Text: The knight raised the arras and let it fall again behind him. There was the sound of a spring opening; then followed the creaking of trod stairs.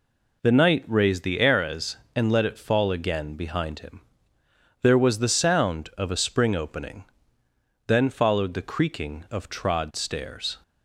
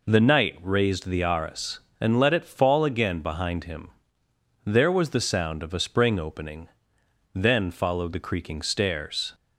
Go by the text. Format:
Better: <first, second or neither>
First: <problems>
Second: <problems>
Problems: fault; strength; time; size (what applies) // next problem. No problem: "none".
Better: first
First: none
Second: skips "of trod"; at 8.6 s